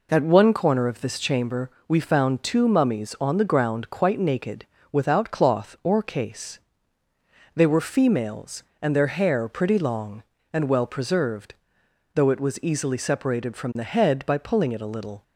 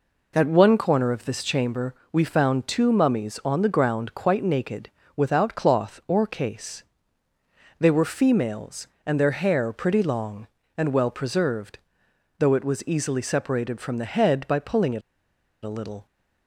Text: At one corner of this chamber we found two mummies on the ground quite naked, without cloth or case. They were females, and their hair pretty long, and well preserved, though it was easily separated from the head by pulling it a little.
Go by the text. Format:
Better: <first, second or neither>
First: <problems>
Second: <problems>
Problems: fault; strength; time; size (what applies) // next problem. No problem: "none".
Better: first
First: pauses between "chamber" and "we"; slight; at 1.6 s; 0.16 s long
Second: pauses between "chamber" and "we"; slight; at 1.9 s; 0.16 s long // pauses between "it" and "a"; noticeable; at 15.0 s; 0.64 s long